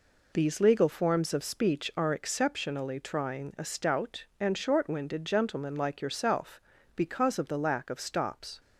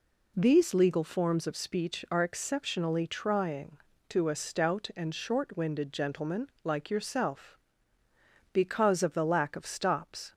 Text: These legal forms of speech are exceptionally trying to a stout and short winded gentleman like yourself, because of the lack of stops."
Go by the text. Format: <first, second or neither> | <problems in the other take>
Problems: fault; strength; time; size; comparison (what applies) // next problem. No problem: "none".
second | skips "to"; at 3.5 s